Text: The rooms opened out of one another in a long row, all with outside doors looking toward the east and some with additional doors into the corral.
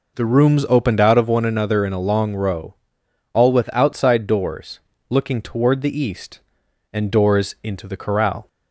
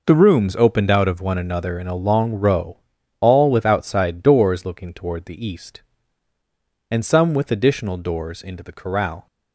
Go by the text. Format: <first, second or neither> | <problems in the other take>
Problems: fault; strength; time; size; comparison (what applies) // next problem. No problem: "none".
second | pauses between "doors" and "looking"; slight; at 4.7 s; 0.30 s long // skips "some with additional"; at 7.1 s